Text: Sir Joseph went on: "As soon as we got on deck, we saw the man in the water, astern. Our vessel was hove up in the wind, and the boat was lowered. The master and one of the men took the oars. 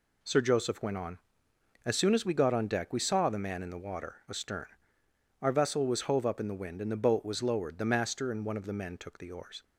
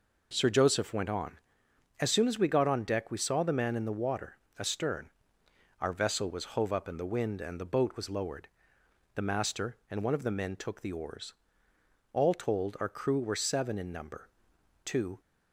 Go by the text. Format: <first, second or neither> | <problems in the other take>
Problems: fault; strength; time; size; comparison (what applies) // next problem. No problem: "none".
first | goes on to say "All told our crew were seven in number Two"; strong; from 12.1 s on; 3.0 s long